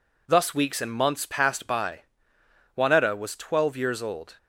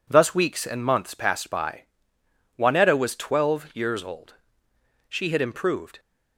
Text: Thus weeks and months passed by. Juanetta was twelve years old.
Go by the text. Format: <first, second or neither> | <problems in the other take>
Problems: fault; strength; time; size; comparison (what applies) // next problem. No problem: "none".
first | goes on to say "She had improved"; noticeable; from 5.0 s on; 0.90 s long